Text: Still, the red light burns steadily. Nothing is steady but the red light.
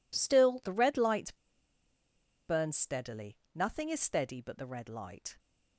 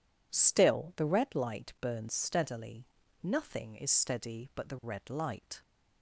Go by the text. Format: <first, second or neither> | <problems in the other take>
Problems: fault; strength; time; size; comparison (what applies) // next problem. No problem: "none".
second | pauses between "light" and "burns"; at 1.3 s; 1.1 s long